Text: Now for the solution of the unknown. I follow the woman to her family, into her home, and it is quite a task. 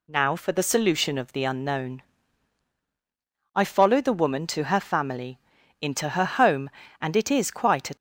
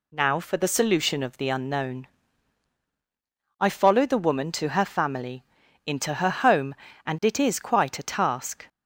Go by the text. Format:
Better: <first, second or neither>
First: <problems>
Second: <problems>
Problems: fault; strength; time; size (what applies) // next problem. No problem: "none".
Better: second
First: stops before "task"; at 7.9 s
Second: none